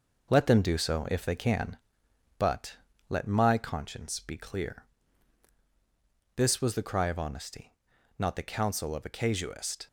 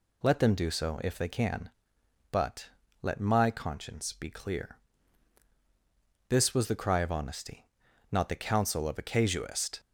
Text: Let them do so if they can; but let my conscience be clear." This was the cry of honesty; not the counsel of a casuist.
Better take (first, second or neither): second